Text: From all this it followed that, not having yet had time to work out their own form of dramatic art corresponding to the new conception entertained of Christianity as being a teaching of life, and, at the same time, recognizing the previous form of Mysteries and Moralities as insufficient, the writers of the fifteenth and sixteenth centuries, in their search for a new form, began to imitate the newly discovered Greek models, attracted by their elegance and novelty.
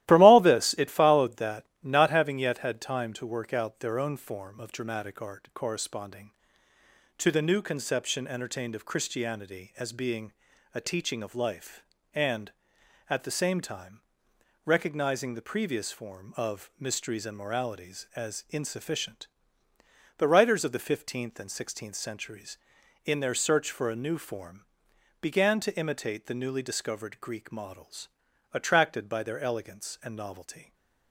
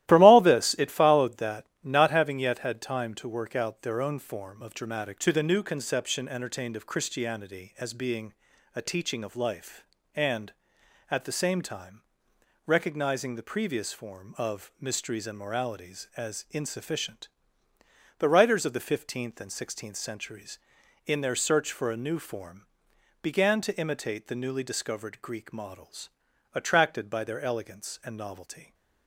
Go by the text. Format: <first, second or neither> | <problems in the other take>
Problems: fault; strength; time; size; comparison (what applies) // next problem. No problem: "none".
first | starts louder than the rest; strong; until 1.1 s; 15 dB; strong in the first // skips "art corresponding"; at 5.1 s // pauses between "being" and "a"; at 8.3 s; 0.42 s long; also in the first